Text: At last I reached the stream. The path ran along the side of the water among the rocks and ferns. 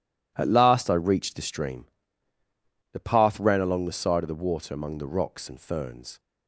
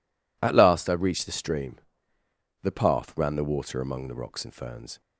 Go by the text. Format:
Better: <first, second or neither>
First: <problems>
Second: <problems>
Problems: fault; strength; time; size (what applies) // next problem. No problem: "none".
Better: first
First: none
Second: skips "along the side of"; at 3.3 s